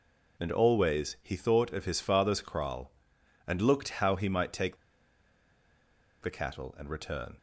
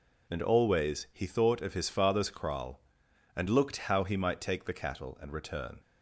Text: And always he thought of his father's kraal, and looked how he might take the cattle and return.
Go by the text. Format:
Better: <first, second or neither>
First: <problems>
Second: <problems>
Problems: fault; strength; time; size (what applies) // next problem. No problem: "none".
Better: second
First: pauses between "take" and "the"; strong; at 4.7 s; 1.4 s long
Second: none